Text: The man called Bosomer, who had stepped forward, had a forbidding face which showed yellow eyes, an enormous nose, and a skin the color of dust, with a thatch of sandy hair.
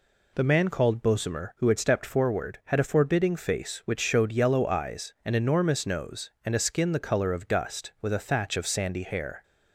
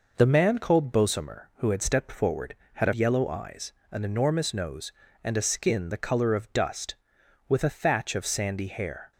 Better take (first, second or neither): first